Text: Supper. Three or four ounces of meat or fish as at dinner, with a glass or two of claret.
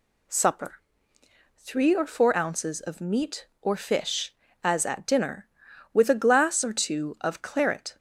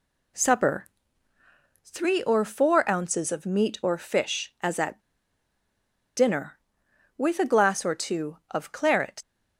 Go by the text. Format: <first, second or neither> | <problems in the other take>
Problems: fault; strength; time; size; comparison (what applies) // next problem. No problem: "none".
first | pauses between "at" and "dinner"; at 4.9 s; 1.1 s long